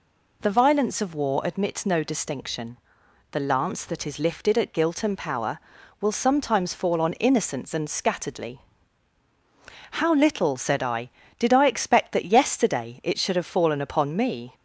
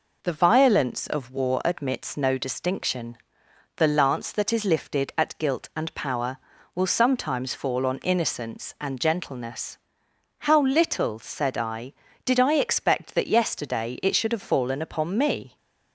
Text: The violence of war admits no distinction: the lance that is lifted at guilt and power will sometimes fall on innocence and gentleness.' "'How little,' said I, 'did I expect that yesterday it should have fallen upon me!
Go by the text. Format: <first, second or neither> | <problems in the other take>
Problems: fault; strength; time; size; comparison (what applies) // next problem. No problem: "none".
second | says "scatteredly" for "gentleness"; at 7.8 s